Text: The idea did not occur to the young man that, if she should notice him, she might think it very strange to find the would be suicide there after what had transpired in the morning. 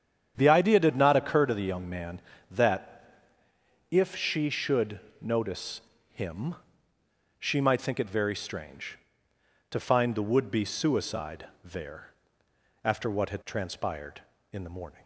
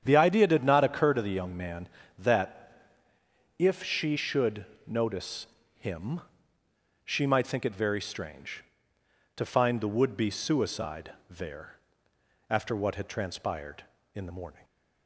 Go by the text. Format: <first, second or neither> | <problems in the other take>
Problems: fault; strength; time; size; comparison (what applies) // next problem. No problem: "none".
neither | starts louder than the rest; strong; the same in both // pauses between "should" and "notice"; slight; the same in both // pauses between "notice" and "him"; slight; the same in both // pauses between "suicide" and "there"; slight; the same in both // pauses between "there" and "after"; noticeable; the same in both